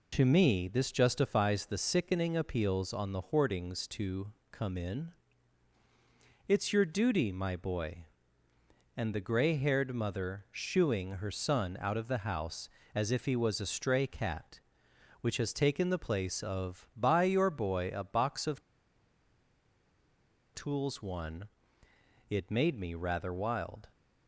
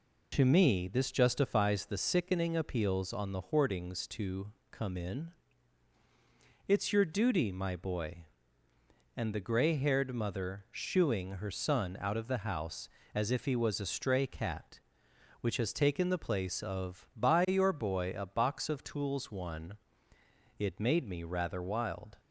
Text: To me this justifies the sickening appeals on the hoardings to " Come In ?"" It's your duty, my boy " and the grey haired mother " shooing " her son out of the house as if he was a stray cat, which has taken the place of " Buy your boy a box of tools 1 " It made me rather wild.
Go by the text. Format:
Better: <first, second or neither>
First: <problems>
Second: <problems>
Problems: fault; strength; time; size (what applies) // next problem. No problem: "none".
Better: second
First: pauses between "of" and "tools"; strong; at 18.6 s; 1.9 s long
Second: none